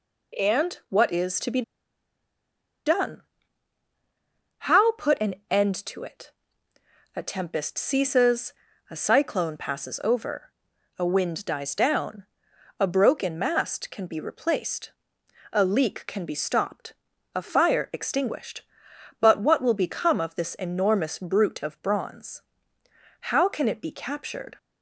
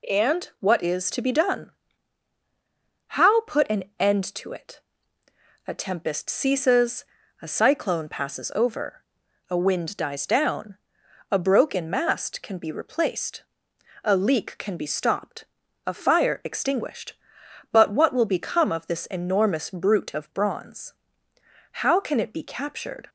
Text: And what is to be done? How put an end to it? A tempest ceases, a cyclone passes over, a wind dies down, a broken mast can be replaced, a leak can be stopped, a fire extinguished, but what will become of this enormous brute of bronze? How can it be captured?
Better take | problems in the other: second | pauses between "be" and "done"; at 1.6 s; 1.2 s long

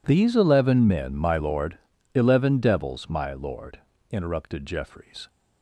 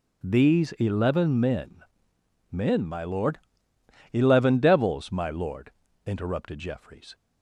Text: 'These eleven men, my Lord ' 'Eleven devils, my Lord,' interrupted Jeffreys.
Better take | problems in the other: first | says "men" twice; at 2.5 s

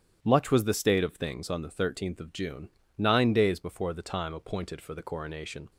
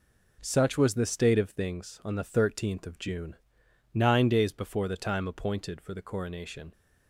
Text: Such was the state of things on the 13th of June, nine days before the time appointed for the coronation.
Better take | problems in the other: second | starts louder than the rest; strong; until 1.2 s; 10 dB // says "Much" for "Such"; at 0.2 s

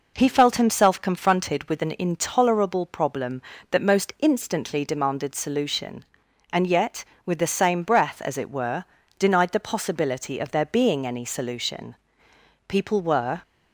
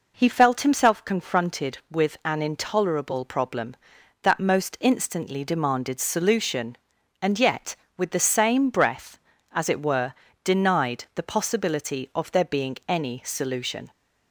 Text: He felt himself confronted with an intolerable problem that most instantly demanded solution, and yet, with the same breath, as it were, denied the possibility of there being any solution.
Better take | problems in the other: second | goes on to say "People were"; noticeable; from 12.6 s on; 0.74 s long

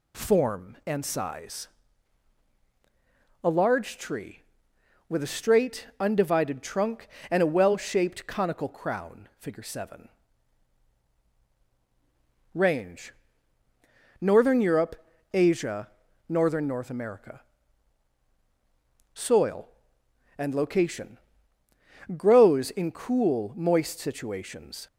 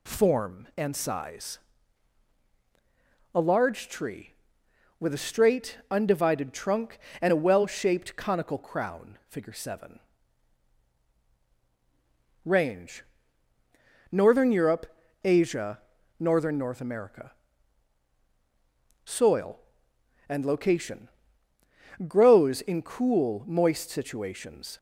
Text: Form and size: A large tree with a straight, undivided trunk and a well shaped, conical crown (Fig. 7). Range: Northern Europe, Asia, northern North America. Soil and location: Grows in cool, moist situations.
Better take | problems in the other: neither | none

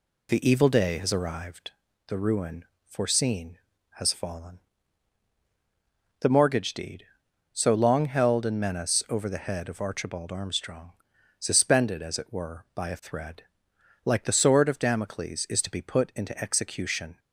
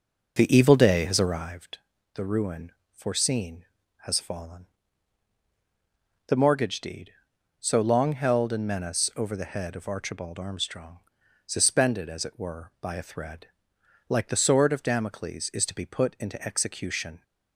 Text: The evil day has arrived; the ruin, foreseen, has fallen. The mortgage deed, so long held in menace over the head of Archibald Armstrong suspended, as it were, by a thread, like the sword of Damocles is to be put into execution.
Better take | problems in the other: first | starts louder than the rest; noticeable; until 1.5 s; 5.5 dB // pauses between "Armstrong" and "suspended"; noticeable; at 10.9 s; 0.48 s long; noticeable in the first

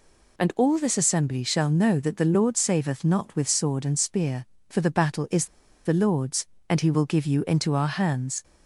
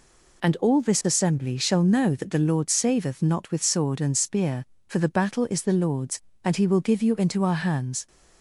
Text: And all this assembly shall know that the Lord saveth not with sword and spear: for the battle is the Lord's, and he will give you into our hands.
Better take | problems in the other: second | pauses between "is" and "the"; at 5.4 s; 0.39 s long

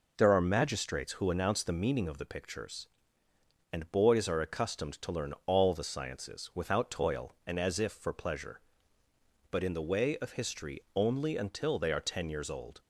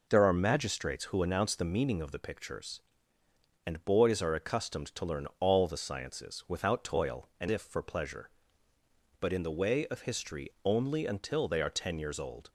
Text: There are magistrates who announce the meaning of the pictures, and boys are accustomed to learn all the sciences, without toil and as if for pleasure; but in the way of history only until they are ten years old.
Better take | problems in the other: first | skips "as"; at 7.4 s

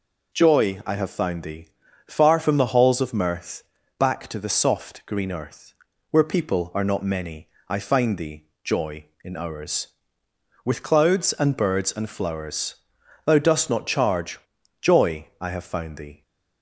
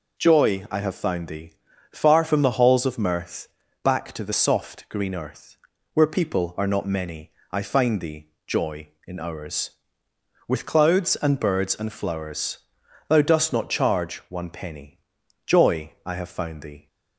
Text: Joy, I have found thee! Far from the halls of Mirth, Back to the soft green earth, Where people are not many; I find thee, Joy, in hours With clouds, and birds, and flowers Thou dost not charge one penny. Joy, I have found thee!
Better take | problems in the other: second | pauses between "flowers" and "Thou"; noticeable; at 12.7 s; 0.50 s long; noticeable in the second // skips "one penny"; at 14.5 s

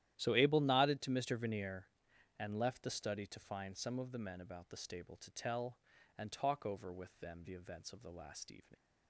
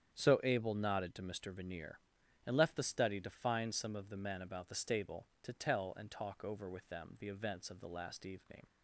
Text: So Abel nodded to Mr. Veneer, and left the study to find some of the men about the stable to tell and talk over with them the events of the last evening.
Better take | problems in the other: second | starts louder than the rest; strong; until 1.1 s; 12.5 dB; strong in the second // leaves "evening" unfinished; at 8.7 s; 90 ms

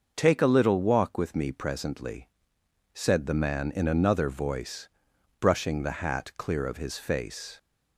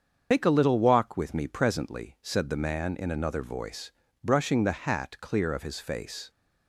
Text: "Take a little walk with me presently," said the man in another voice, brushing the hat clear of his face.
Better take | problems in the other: first | loses the start of "Take"; at 0.3 s; 90 ms // starts louder than the rest; until 1.3 s; 7 dB

